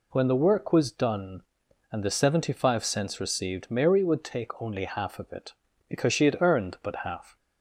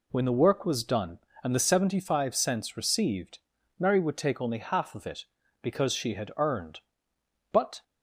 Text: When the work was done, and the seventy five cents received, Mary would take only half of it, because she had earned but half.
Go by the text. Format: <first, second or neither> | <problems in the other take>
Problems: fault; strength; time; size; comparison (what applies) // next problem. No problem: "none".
first | stops before "half"; at 7.8 s